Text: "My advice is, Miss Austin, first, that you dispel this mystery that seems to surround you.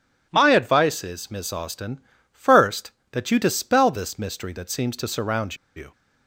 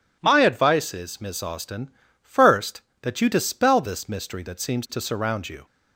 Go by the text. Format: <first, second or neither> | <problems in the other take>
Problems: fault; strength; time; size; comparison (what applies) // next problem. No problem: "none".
second | pauses between "surround" and "you"; slight; at 5.5 s; 0.19 s long